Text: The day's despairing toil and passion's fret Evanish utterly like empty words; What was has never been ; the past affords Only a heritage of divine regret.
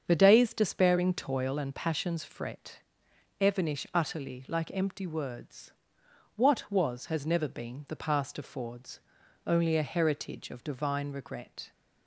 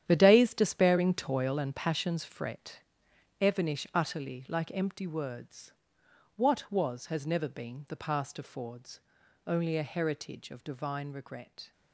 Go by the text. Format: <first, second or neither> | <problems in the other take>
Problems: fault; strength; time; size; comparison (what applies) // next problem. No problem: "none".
first | gets quieter; strong; throughout; 12.5 dB // starts louder than the rest; strong; until 1.0 s; 10 dB; strong in the first // pauses between "fret" and "Evanish"; noticeable; at 2.8 s; 0.60 s long; noticeable in the first // pauses between "affords" and "Only"; noticeable; at 8.9 s; 0.48 s long; noticeable in the first